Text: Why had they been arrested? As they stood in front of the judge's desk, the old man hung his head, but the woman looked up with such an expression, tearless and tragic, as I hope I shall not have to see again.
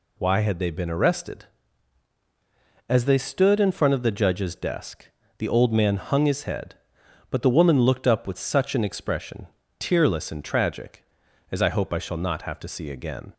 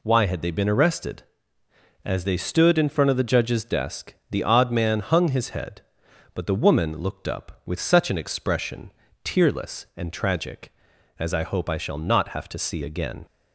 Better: first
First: none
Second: says "odd" for "old"; at 4.4 s

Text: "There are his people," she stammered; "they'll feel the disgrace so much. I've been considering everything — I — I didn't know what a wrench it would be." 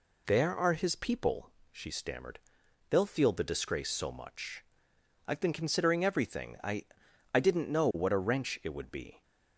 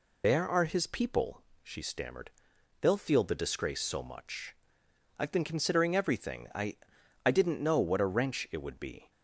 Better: first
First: none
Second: loses the start of "There"; at 0.2 s; 45 ms

